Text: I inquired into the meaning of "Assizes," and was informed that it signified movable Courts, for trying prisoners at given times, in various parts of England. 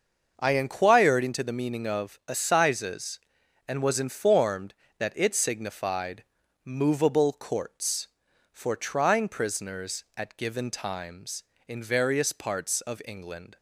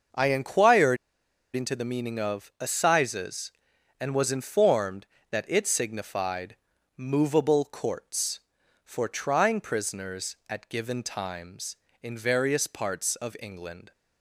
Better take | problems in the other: first | starts louder than the rest; until 1.7 s; 6 dB; also in the first // pauses between "inquired" and "into"; noticeable; at 0.9 s; 0.58 s long // pauses between "signified" and "movable"; at 6.5 s; 0.40 s long; also in the first

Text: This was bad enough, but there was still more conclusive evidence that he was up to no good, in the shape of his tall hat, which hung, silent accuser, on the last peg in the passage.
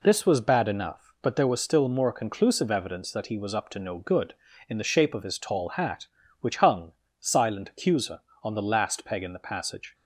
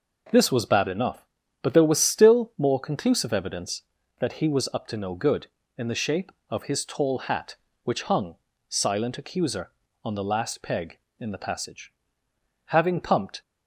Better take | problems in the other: first | goes on to say "Having pumped"; noticeable; from 12.6 s on; 0.76 s long

